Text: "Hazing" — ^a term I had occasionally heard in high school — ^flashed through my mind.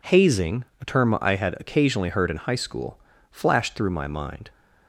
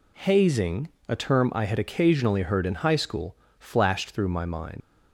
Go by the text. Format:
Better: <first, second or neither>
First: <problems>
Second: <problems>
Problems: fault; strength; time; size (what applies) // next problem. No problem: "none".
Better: first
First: none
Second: leaves "mind" unfinished; at 4.8 s; 90 ms